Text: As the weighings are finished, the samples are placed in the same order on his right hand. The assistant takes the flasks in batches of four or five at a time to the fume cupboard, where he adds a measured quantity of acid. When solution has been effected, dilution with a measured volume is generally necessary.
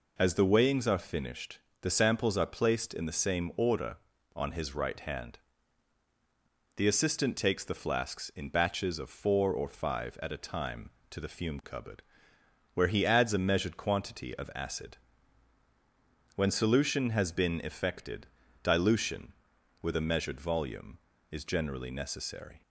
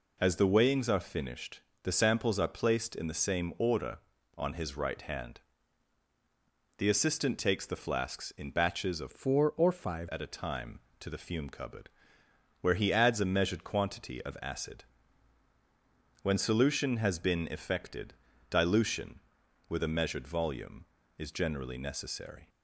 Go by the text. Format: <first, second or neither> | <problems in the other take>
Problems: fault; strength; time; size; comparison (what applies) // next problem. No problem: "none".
first | changes voice from "four" to "five"; from 9.1 to 10.0 s; 0.9 s long